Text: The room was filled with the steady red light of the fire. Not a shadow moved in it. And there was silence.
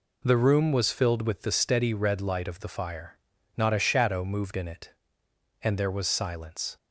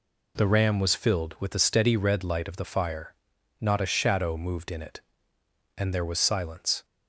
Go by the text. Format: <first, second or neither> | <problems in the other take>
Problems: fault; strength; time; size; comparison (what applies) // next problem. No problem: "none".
first | says "ram" for "room"; at 0.4 s